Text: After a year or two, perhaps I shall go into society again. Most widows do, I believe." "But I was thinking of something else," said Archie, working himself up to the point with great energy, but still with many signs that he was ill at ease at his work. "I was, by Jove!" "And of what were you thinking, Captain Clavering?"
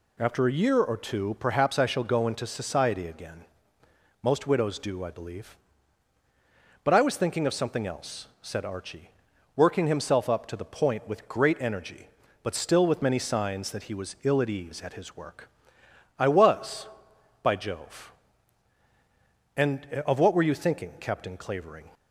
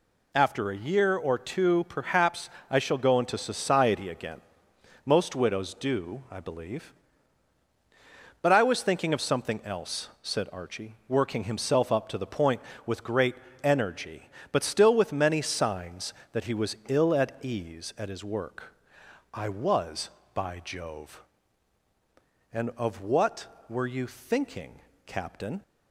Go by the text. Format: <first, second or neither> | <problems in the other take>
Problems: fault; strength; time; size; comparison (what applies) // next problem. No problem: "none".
first | pauses between "perhaps" and "I"; slight; at 2.4 s; 0.22 s long // pauses between "great" and "energy"; slight; at 13.3 s; 0.28 s long // stops before "Clavering"; at 25.6 s